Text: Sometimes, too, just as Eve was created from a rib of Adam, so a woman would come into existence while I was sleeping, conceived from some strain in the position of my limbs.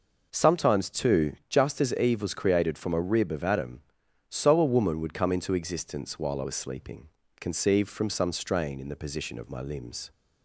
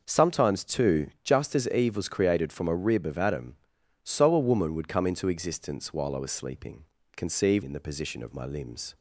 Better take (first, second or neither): first